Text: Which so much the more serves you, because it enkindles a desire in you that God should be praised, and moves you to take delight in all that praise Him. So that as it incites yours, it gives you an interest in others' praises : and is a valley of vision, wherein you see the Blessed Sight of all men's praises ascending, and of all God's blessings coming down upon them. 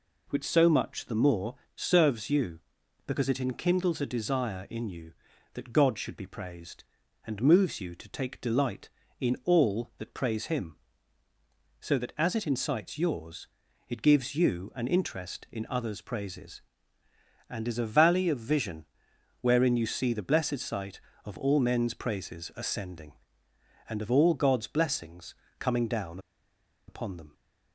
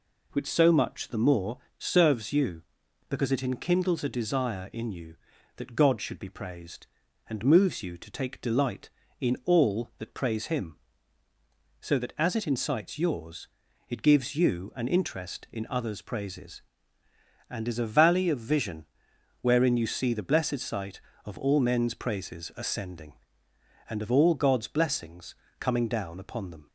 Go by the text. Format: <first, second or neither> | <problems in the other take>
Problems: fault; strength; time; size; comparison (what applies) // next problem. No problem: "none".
second | pauses between "more" and "serves"; slight; at 1.5 s; 0.20 s long; slight in the second // pauses between "blessings" and "coming"; slight; at 25.3 s; 0.26 s long; slight in the second // pauses between "down" and "upon"; noticeable; at 26.1 s; 0.69 s long